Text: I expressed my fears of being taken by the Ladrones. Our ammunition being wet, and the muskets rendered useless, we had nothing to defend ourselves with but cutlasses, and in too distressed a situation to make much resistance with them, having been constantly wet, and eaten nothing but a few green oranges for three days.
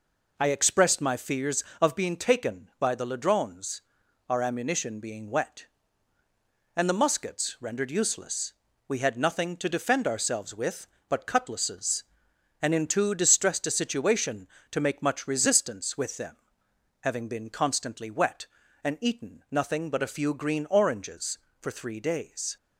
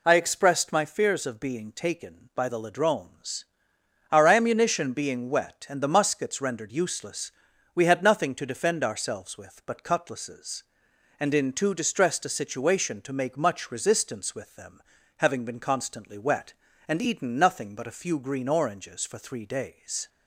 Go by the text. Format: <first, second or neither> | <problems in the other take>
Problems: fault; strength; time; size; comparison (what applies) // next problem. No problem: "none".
neither | none